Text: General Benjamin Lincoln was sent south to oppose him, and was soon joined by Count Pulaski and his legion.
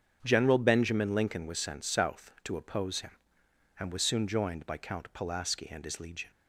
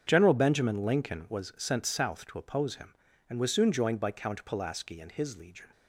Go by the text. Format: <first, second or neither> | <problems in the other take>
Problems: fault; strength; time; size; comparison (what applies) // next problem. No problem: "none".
neither | starts louder than the rest; strong; the same in both